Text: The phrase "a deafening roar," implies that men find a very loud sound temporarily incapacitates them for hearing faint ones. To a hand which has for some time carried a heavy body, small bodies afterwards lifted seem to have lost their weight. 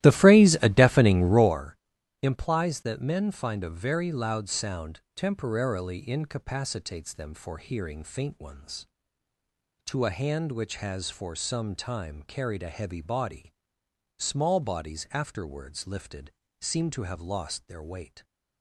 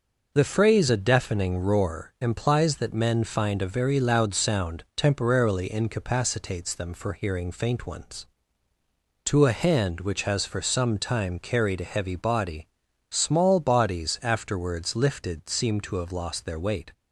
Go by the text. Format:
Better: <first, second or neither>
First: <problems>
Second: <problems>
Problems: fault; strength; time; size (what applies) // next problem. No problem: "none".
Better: second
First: starts louder than the rest; strong; until 1.6 s; 15 dB // pauses between "sound" and "temporarily"; slight; at 4.9 s; 0.16 s long // pauses between "lifted" and "seem"; slight; at 16.2 s; 0.30 s long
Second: none